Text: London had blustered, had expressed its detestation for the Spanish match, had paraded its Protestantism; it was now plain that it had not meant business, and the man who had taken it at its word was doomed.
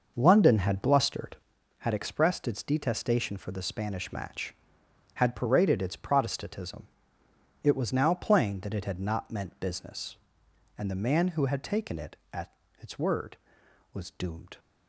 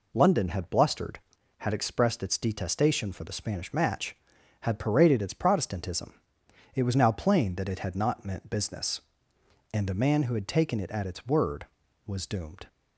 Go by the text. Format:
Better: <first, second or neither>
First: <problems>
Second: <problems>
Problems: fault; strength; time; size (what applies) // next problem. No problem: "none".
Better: second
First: starts louder than the rest; noticeable; until 1.8 s; 6 dB // pauses between "at" and "its"; slight; at 12.5 s; 0.26 s long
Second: none